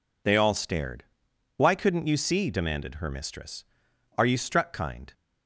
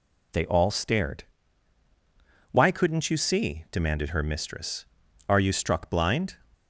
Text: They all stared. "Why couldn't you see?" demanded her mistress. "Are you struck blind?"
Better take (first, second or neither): second